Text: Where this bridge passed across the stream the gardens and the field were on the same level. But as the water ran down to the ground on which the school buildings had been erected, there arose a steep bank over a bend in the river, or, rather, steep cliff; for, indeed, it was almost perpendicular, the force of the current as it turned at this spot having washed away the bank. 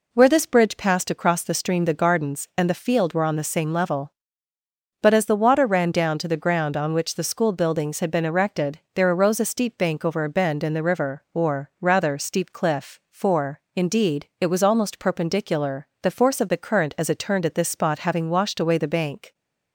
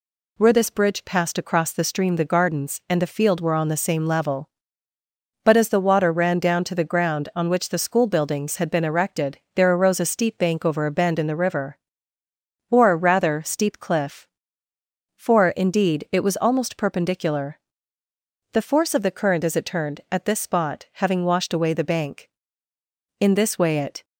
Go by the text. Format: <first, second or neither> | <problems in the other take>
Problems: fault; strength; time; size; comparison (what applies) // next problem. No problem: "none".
first | goes on to say "In this way it"; noticeable; from 23.2 s on; 0.84 s long